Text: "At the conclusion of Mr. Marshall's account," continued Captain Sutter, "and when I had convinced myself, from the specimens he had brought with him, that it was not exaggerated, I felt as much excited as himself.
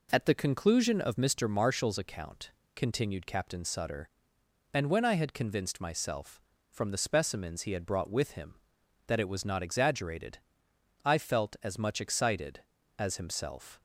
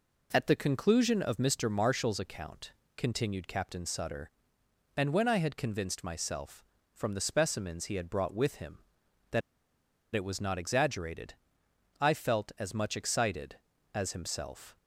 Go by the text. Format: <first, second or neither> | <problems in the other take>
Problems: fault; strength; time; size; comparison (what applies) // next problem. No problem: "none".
first | pauses between "that" and "it"; noticeable; at 9.4 s; 0.74 s long